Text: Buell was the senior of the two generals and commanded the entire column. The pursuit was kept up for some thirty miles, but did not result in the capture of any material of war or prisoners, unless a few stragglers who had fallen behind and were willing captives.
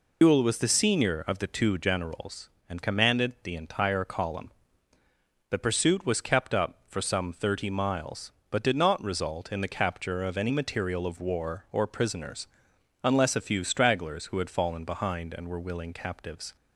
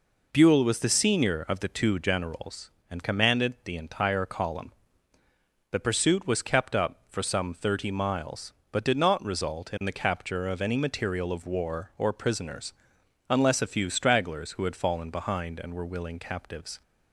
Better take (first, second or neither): second